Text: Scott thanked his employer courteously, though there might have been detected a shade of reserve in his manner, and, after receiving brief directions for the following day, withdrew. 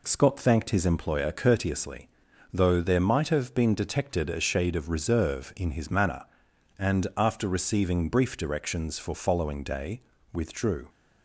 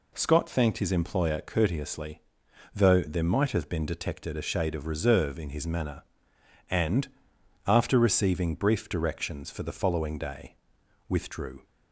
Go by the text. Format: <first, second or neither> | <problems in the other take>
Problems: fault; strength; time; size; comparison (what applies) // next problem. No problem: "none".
second | skips "the"; at 9.1 s